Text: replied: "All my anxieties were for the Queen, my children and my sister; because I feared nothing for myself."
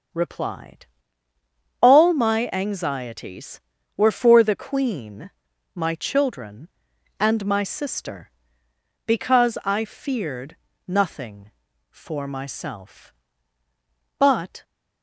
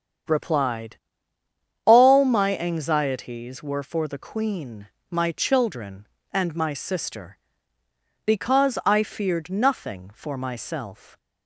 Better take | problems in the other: second | starts louder than the rest; strong; until 2.1 s; 7 dB; strong in the second // pauses between "feared" and "nothing"; slight; at 10.5 s; 0.32 s long // goes on to say "But"; slight; from 14.1 s on; 0.46 s long

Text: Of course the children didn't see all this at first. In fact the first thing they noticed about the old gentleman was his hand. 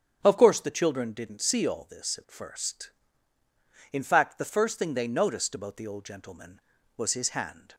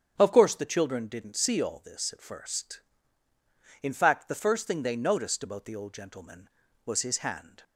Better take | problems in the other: neither | starts louder than the rest; strong; the same in both

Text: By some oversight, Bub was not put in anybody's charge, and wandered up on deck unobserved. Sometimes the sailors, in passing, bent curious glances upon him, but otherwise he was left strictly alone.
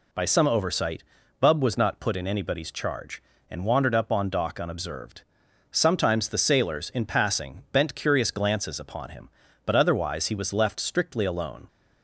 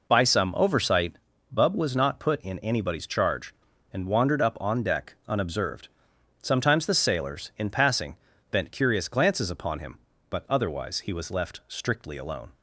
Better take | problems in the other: second | says "dock" for "deck"; at 4.2 s

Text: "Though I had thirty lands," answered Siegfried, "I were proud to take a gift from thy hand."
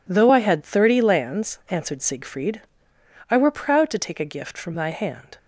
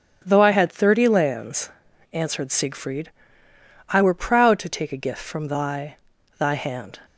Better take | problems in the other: first | starts louder than the rest; strong; until 1.2 s; 9 dB // says "thy" twice; at 6.3 s

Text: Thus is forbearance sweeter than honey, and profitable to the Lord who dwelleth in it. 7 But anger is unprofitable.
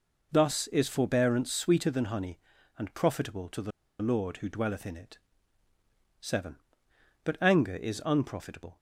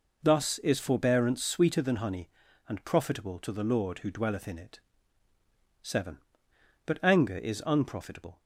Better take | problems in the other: second | pauses between "the" and "Lord"; slight; at 3.7 s; 0.31 s long

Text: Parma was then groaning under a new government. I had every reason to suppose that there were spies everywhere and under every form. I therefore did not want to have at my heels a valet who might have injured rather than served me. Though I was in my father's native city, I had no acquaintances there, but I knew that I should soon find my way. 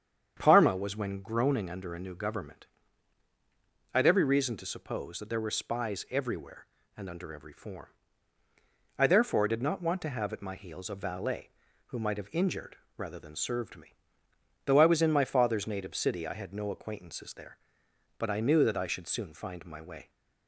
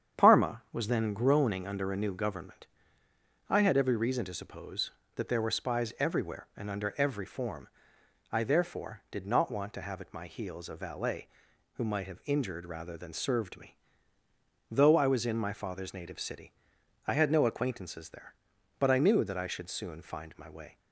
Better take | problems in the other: second | starts louder than the rest; strong; until 1.3 s; 8 dB; strong in the second // says "when" for "then"; at 0.9 s // pauses between "injured" and "rather"; slight; at 12.7 s; 0.20 s long

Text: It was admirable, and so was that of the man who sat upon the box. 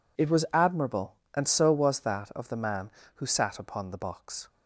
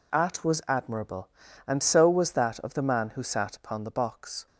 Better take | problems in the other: first | says "At" for "It"; at 0.1 s

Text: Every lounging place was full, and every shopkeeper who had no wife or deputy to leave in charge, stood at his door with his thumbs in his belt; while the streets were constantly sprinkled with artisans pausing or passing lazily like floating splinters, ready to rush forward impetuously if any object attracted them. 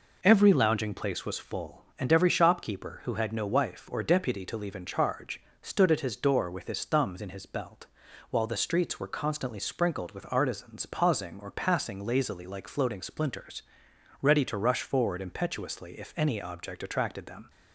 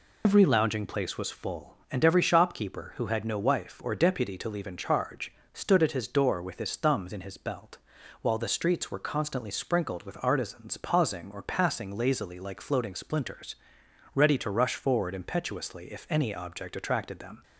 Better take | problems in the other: first | loses the start of "Every"; at 0.2 s; 95 ms

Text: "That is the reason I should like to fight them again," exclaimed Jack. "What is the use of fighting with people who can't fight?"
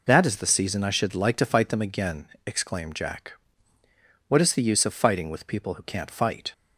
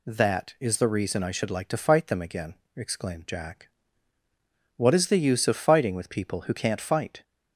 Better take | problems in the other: second | says "season" for "reason"; at 0.4 s

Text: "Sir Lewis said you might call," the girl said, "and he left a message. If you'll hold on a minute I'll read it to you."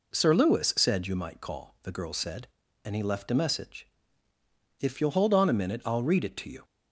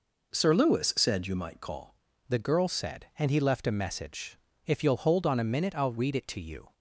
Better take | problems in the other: first | changes voice at "the"; from 2.2 s on; 4.5 s long

